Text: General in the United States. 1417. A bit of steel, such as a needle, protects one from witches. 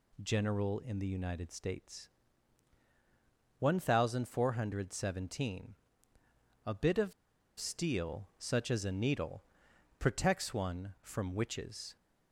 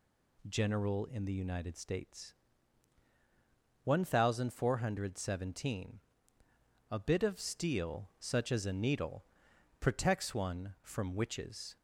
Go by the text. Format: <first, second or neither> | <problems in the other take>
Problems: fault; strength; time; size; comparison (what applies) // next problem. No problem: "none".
second | pauses between "of" and "steel"; noticeable; at 7.1 s; 0.46 s long